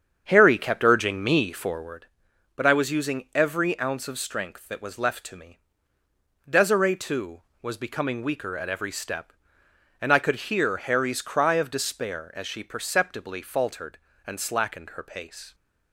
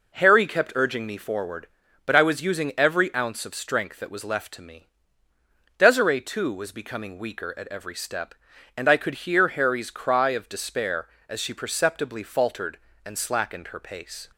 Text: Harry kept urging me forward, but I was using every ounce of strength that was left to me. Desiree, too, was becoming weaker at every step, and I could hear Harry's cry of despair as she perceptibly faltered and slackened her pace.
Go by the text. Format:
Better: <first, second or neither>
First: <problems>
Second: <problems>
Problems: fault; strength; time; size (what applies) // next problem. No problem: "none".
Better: second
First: starts louder than the rest; strong; until 2.1 s; 7.5 dB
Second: none